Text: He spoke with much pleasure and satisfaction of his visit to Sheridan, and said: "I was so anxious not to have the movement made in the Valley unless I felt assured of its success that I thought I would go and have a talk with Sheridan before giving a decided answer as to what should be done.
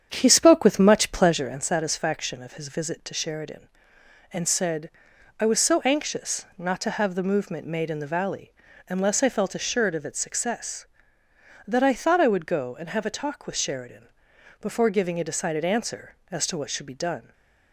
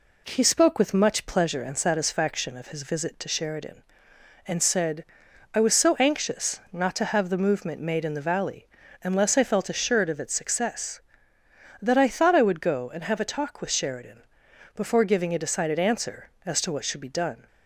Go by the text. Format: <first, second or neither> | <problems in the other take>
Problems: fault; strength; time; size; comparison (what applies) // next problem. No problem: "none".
second | starts louder than the rest; strong; until 1.6 s; 8.5 dB // pauses between "Valley" and "unless"; slight; at 8.5 s; 0.36 s long; slight in the second // pauses between "Sheridan" and "before"; noticeable; at 14.0 s; 0.52 s long; noticeable in the second // stays silent after the last word; slight; from 17.2 s on; 0.5 s long